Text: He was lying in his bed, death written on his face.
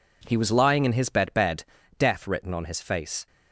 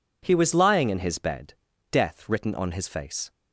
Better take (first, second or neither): second